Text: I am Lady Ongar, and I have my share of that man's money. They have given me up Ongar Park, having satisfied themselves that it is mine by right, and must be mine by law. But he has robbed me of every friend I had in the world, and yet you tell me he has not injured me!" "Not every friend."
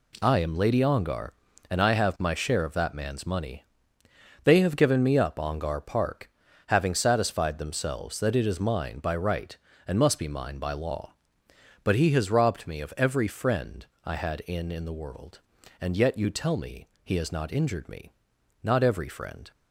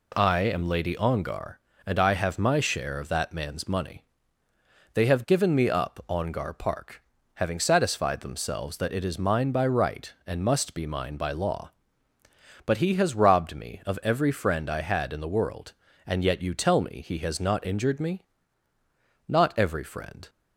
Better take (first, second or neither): second